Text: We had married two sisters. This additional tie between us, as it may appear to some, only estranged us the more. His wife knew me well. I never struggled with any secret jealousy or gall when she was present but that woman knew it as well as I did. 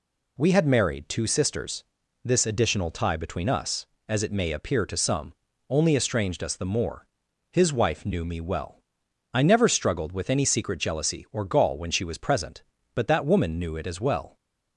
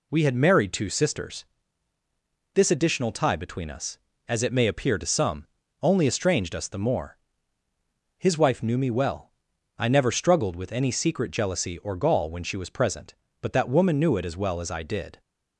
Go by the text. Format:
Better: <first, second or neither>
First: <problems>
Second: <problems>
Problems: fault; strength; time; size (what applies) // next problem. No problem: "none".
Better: second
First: stops before "as I did"; at 14.3 s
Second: none